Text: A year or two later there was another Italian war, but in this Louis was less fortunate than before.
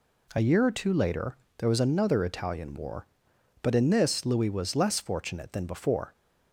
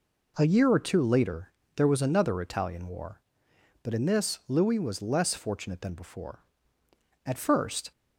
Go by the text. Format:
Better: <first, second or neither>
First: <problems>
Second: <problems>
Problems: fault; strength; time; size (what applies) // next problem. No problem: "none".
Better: first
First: pauses between "later" and "there"; slight; at 1.3 s; 0.20 s long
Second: pauses between "later" and "there"; slight; at 1.5 s; 0.24 s long // goes on to say "At first"; noticeable; from 7.2 s on; 0.66 s long